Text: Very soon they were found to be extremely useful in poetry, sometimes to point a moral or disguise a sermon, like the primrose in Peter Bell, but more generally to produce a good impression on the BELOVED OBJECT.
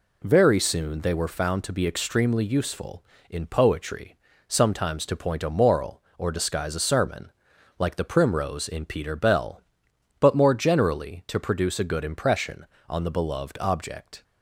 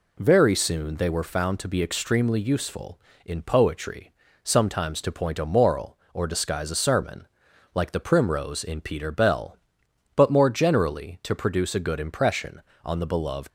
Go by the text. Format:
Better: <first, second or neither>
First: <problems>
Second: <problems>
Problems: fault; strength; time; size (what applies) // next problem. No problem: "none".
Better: first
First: none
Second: stops before "OBJECT"; at 13.4 s